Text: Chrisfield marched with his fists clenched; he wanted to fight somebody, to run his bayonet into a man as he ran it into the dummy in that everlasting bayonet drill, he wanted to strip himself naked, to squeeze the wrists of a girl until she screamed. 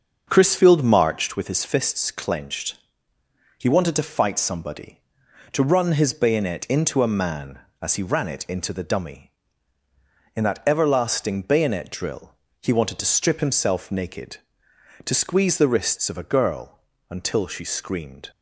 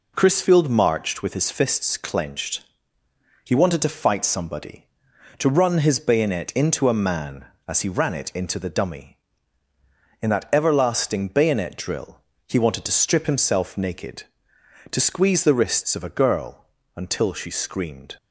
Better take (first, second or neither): second